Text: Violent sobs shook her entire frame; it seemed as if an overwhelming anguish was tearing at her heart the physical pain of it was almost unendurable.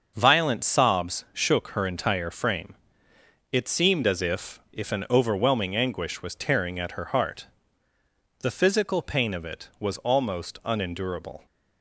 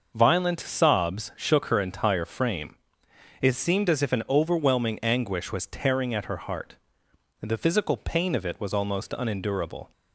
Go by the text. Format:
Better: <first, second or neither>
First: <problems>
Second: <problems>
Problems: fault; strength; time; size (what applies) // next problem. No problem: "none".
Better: second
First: starts louder than the rest; until 1.1 s; 6 dB // says "if" twice; at 4.7 s // pauses between "heart" and "the"; noticeable; at 7.4 s; 0.94 s long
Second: starts louder than the rest; noticeable; until 1.1 s; 6 dB // pauses between "heart" and "the"; noticeable; at 6.7 s; 0.64 s long